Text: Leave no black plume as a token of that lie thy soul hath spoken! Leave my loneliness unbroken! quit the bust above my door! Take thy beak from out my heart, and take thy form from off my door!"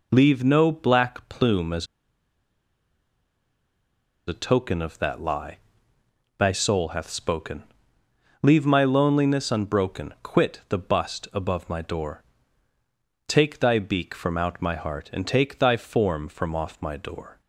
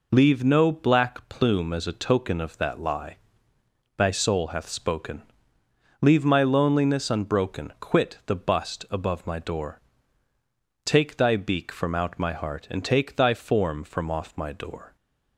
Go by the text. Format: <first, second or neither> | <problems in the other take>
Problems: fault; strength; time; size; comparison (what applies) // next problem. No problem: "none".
second | pauses between "as" and "a"; strong; at 1.8 s; 2.4 s long // pauses between "lie" and "thy"; noticeable; at 5.5 s; 0.80 s long; noticeable in the second